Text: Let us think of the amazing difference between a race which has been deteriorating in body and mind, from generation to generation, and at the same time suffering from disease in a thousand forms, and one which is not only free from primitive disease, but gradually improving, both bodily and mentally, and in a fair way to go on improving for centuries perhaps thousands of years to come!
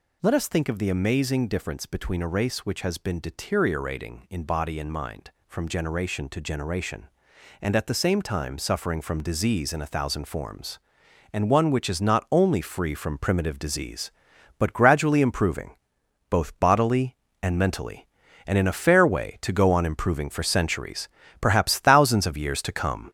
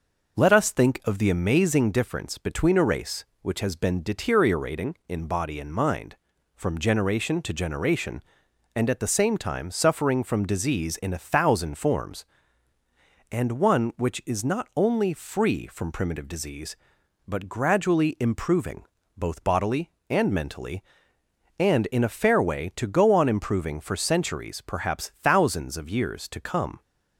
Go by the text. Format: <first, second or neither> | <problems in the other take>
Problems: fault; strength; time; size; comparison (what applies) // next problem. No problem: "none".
second | gets louder; noticeable; throughout; 5.5 dB // pauses between "centuries" and "perhaps"; slight; at 21.0 s; 0.32 s long